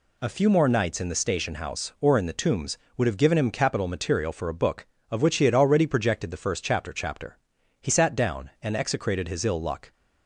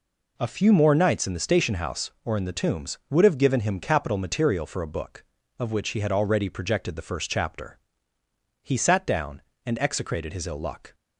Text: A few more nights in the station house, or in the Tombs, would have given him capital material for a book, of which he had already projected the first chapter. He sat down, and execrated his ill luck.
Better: second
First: says "chapter" twice; at 6.9 s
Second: none

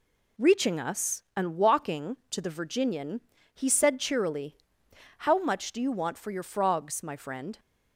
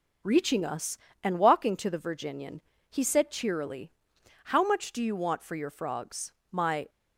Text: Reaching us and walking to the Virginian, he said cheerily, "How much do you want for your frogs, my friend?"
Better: first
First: none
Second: stops before "friend"; at 6.8 s

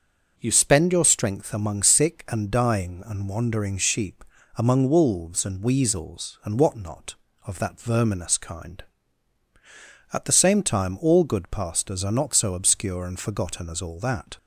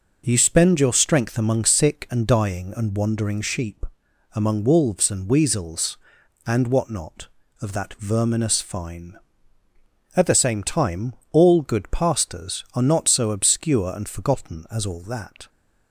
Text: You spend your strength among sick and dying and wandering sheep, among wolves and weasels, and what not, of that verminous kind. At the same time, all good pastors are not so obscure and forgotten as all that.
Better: first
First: none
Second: says "fine" for "kind"; at 8.6 s

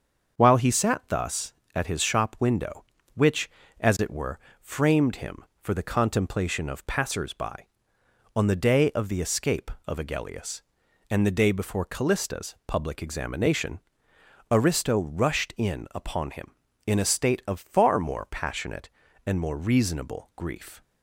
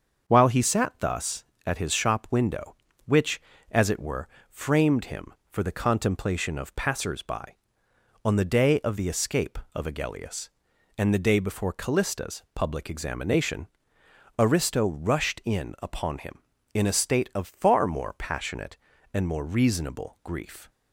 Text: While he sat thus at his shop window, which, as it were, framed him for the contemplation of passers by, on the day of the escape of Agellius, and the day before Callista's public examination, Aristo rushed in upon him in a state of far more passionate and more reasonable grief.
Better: neither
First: starts louder than the rest; until 1.4 s; 6.5 dB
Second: starts louder than the rest; until 1.3 s; 6.5 dB

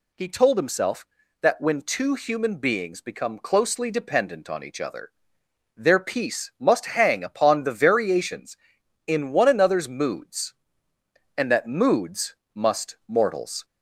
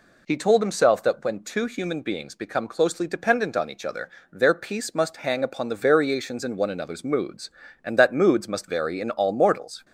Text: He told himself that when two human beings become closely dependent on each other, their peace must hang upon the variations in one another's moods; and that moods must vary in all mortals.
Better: second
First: pauses between "moods" and "must"; slight; at 12.3 s; 0.18 s long // skips "vary in all"; at 13.0 s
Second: none

